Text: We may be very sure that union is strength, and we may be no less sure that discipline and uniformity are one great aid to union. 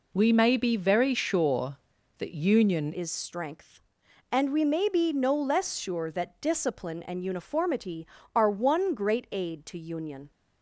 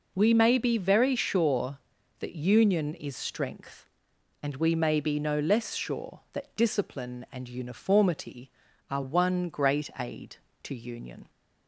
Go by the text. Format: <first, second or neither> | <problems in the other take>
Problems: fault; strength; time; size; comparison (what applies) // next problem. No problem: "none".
second | changes voice at "is"; from 2.9 s on; 7.4 s long